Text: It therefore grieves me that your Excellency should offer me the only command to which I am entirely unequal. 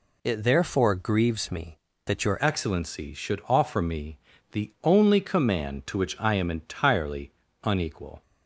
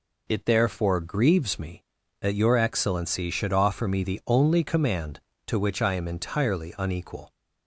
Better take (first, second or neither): second